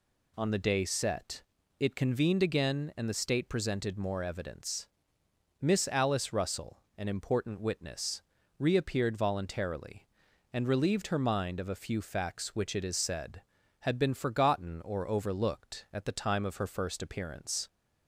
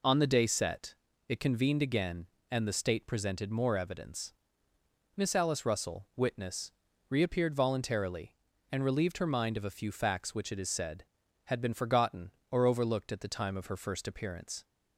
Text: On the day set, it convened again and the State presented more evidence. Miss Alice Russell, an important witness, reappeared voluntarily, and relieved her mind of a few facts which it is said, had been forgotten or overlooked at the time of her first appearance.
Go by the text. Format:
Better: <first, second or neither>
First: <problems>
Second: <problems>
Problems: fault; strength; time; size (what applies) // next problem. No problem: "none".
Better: first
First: none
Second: skips "an important"; at 6.1 s